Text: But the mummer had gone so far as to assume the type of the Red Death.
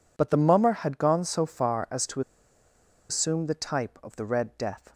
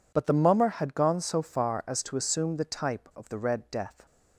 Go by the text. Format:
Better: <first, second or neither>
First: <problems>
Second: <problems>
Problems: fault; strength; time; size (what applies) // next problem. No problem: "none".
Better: second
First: pauses between "to" and "assume"; noticeable; at 2.2 s; 0.89 s long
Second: none